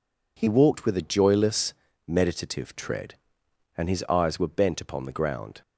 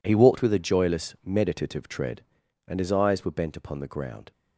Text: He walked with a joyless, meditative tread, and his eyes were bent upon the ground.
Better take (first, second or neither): first